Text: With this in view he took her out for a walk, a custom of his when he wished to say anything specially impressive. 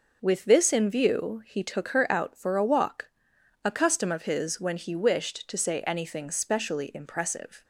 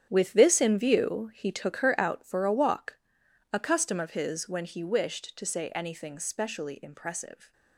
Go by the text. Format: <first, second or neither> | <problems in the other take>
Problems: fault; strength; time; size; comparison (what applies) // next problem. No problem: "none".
first | gets quieter; strong; throughout; 12 dB